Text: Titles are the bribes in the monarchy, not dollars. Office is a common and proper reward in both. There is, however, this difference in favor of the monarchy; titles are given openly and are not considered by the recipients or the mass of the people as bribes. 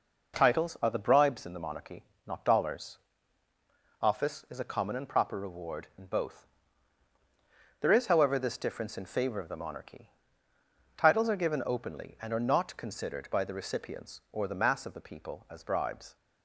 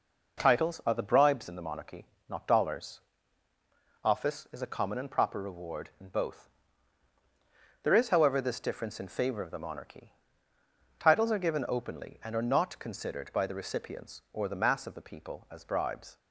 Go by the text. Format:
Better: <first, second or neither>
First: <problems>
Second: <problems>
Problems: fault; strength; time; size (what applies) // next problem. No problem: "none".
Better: neither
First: none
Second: none